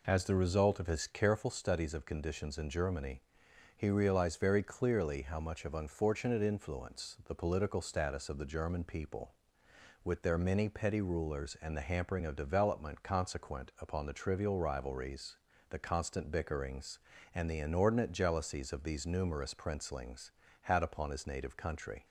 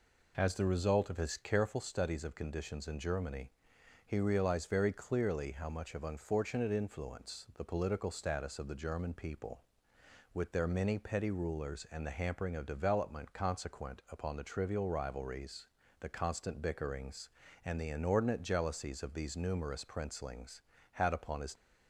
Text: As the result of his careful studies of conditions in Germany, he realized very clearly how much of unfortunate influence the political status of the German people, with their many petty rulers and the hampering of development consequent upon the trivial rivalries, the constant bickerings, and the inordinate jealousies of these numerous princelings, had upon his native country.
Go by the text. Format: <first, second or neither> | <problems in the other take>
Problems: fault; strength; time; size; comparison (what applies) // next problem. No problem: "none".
first | stops before "native country"; at 21.5 s